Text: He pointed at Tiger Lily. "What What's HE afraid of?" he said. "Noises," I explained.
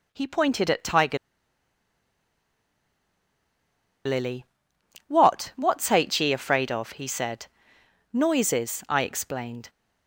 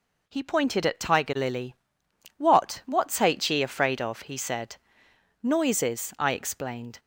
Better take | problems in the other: second | pauses between "Tiger" and "Lily"; strong; at 1.1 s; 2.9 s long

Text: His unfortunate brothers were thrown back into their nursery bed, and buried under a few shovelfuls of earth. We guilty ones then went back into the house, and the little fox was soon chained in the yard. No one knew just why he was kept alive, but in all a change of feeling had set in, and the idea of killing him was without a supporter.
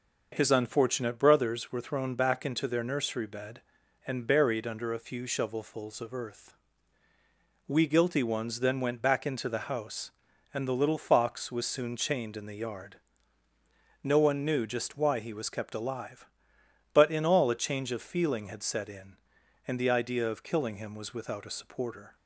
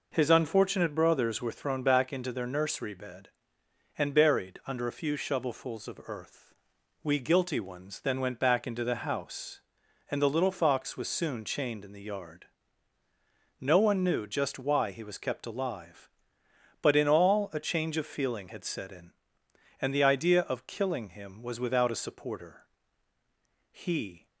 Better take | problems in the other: first | goes on to say "He"; from 23.7 s on; 0.56 s long

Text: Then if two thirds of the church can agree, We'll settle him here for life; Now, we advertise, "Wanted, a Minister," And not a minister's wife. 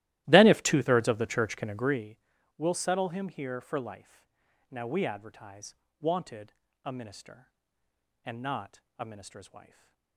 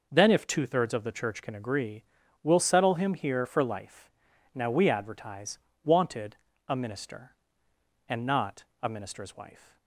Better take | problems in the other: second | starts louder than the rest; strong; until 2.2 s; 15.5 dB // pauses between "not" and "a"; slight; at 8.8 s; 0.18 s long; slight in the second // stays silent after the last word; slight; from 9.6 s on; 0.5 s long

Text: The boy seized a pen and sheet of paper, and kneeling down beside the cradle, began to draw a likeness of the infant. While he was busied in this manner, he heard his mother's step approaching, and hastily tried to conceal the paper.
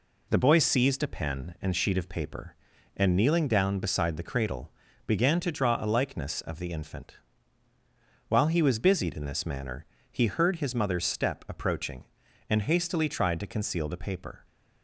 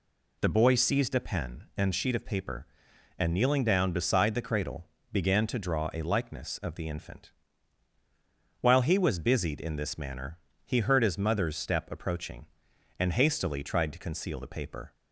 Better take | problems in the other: neither | none

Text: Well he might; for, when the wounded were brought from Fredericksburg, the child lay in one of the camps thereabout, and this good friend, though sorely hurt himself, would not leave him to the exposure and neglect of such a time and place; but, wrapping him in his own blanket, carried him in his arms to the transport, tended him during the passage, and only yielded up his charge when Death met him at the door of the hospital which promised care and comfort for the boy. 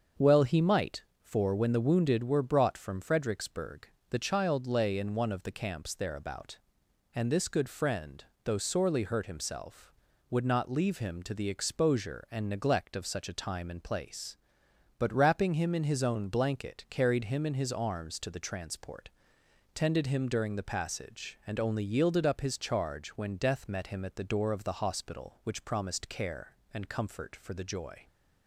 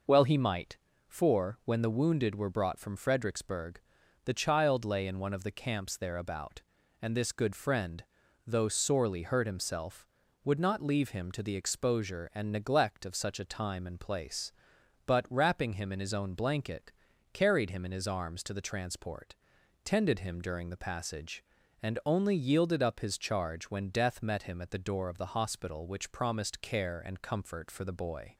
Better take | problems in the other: second | starts louder than the rest; until 1.3 s; 6.5 dB // says "joy" for "boy"; at 27.6 s

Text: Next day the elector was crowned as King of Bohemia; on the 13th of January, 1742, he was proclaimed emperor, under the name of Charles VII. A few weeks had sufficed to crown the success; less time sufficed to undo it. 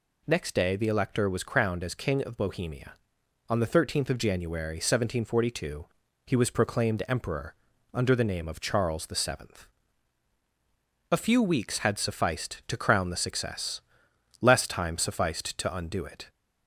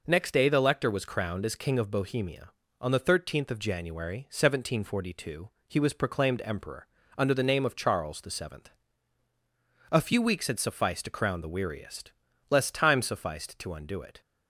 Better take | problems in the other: first | says "weariest" for "success"; at 11.4 s

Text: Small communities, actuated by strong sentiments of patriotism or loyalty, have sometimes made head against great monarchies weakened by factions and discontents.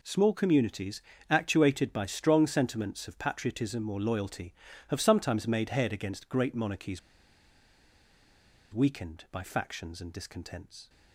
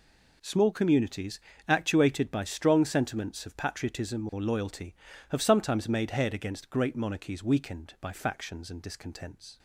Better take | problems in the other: second | pauses between "monarchies" and "weakened"; strong; at 6.9 s; 1.7 s long

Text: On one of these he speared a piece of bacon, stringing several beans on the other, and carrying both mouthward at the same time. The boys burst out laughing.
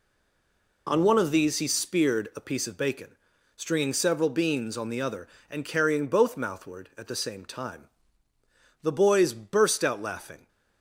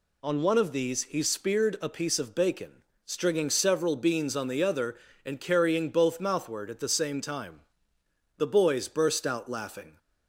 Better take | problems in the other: second | stays silent before the first word; slight; until 0.8 s; 0.8 s long

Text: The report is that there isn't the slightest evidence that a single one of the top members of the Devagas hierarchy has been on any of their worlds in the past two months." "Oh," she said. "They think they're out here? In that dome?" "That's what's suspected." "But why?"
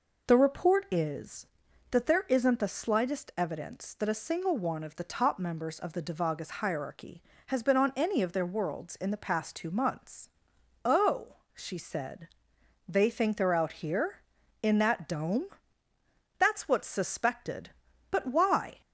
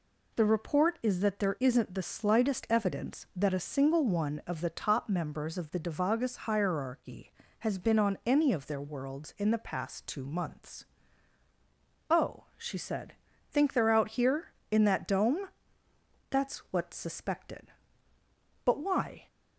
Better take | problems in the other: first | skips "They"; at 13.3 s

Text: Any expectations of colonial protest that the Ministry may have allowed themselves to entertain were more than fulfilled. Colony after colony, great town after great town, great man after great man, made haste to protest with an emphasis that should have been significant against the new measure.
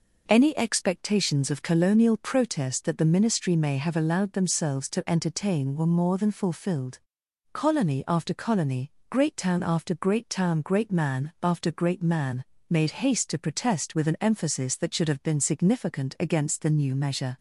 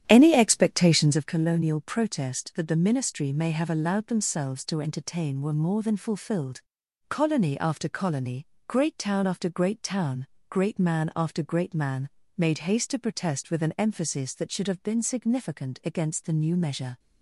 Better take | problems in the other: first | starts louder than the rest; strong; until 1.3 s; 10.5 dB

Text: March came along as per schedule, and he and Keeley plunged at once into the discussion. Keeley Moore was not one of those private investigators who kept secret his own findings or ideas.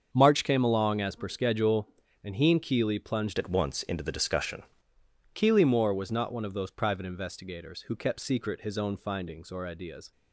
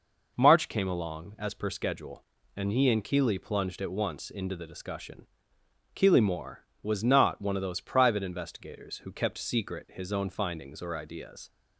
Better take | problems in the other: second | starts louder than the rest; until 1.1 s; 7 dB // changes voice from "at" to "discussion"; from 3.3 to 4.6 s; 1.3 s long

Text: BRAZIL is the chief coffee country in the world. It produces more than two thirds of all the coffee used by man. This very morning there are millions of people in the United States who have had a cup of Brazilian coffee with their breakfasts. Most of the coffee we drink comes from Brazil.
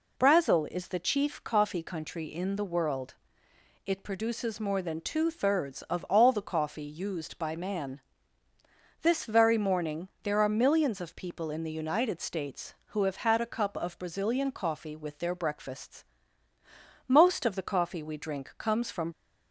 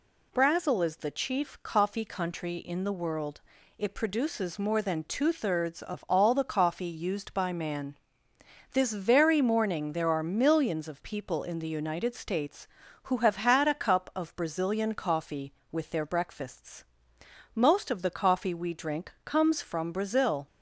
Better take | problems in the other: second | stops before "Brazil"; at 19.1 s

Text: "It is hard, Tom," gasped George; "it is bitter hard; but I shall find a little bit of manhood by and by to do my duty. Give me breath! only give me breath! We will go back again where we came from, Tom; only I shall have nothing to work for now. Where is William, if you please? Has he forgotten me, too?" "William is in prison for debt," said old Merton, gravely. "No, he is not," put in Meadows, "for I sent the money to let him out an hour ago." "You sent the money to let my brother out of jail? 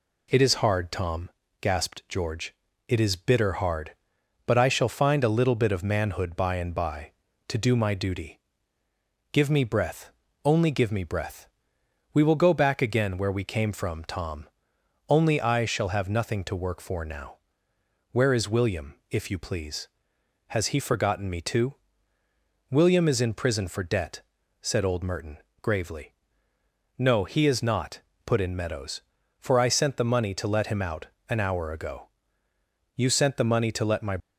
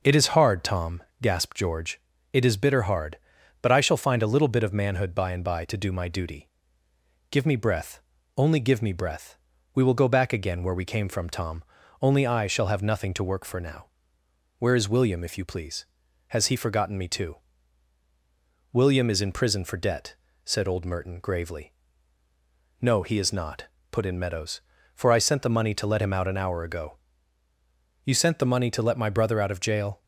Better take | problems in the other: second | pauses between "out" and "an"; slight; at 31.0 s; 0.20 s long // stops before "brother out of jail"; at 34.2 s

